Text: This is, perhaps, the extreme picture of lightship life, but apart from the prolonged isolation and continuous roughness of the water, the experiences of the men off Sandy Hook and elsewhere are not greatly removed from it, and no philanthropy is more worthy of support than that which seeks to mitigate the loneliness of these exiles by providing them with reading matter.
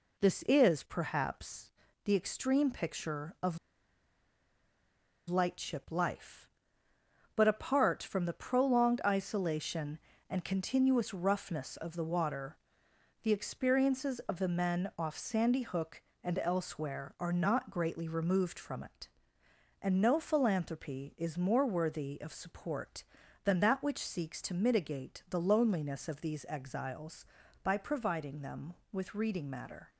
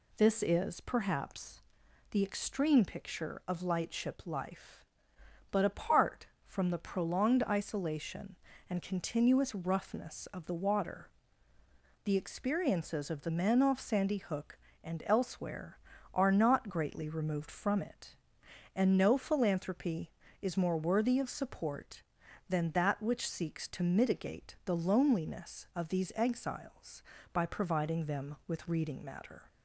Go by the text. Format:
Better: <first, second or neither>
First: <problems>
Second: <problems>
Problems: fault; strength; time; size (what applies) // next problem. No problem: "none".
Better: second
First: pauses between "of" and "lightship"; strong; at 3.5 s; 1.7 s long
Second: none